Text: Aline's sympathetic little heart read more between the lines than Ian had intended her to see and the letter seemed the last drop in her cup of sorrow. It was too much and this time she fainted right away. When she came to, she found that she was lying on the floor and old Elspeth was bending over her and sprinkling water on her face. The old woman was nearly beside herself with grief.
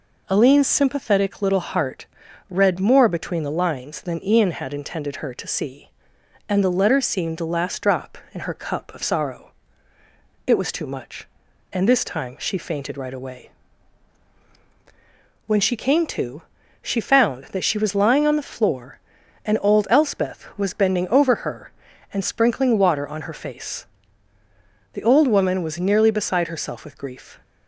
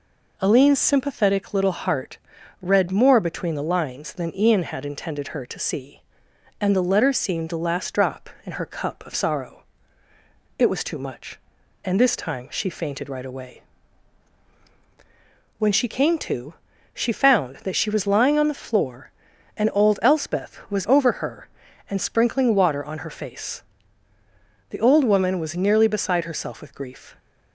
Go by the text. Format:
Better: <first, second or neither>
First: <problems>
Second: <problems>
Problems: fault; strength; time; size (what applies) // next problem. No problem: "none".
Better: first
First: pauses between "heart" and "read"; at 2.0 s; 0.42 s long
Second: pauses between "heart" and "read"; at 2.1 s; 0.42 s long // skips "bending"; at 20.8 s